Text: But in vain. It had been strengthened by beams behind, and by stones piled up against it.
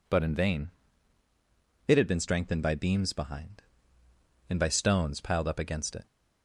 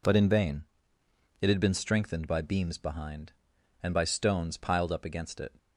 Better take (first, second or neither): neither